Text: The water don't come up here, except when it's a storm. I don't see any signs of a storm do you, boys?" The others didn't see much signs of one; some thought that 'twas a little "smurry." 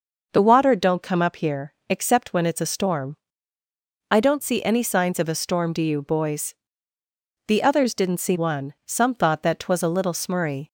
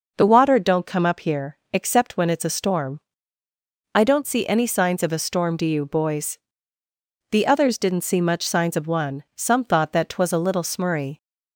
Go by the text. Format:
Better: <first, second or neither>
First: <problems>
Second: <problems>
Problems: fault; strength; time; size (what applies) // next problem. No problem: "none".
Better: second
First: skips "much signs of"; at 8.3 s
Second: none